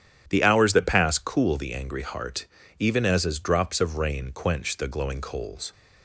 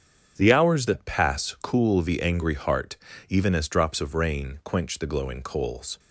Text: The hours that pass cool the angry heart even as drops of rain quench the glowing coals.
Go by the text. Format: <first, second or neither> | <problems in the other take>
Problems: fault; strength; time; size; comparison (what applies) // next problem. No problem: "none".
second | starts louder than the rest; strong; until 1.3 s; 10 dB; strong in the second // pauses between "heart" and "even"; slight; at 2.4 s; 0.32 s long; slight in the second // says "as" twice; at 3.2 s